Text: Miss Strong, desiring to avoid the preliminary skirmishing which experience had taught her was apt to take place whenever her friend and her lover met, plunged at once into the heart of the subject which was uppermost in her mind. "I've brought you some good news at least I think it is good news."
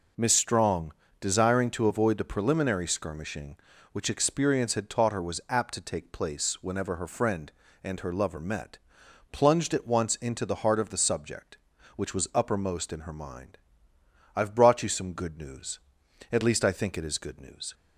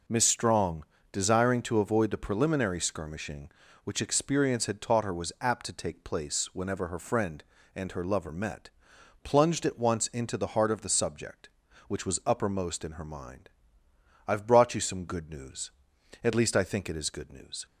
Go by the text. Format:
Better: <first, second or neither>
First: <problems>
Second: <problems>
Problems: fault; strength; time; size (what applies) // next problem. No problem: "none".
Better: neither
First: none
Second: none